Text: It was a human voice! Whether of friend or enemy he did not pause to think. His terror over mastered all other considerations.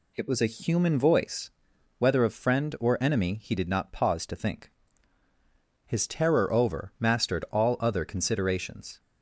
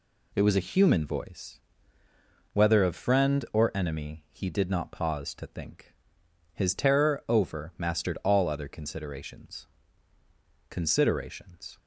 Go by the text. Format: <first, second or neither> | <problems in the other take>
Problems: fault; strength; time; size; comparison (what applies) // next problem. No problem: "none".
first | says "considerations" twice; at 10.6 s